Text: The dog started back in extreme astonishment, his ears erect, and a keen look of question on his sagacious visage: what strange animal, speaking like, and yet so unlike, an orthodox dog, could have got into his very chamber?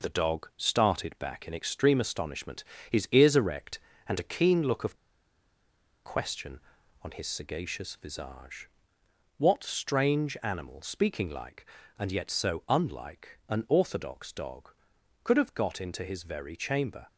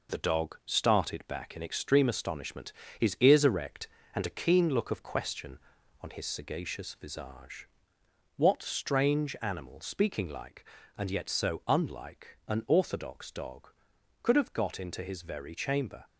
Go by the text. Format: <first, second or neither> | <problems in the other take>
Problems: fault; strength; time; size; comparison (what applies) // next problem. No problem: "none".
second | pauses between "of" and "question"; at 4.9 s; 1.0 s long